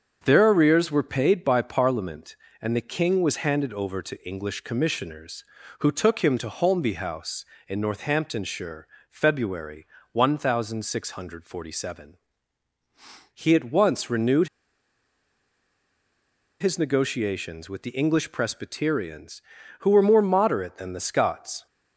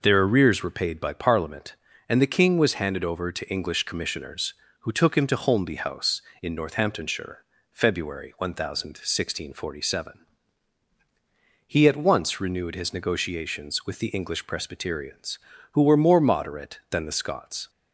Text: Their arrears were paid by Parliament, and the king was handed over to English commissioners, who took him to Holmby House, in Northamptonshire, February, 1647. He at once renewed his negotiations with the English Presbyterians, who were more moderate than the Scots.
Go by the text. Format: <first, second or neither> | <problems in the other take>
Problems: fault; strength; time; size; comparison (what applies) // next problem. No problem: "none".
second | starts louder than the rest; until 1.2 s; 6.5 dB // pauses between "renewed" and "his"; strong; at 14.4 s; 2.1 s long